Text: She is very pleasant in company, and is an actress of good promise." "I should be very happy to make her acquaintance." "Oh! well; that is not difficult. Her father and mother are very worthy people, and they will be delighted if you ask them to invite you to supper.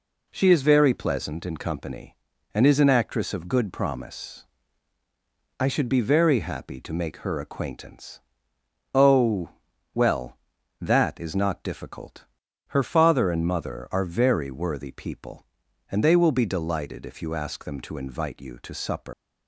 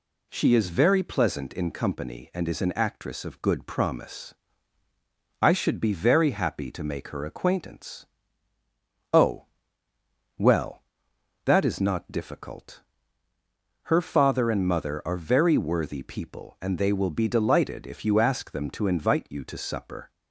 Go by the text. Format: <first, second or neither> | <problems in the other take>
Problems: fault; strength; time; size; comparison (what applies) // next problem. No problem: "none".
second | leaves "supper" unfinished; at 19.1 s; 130 ms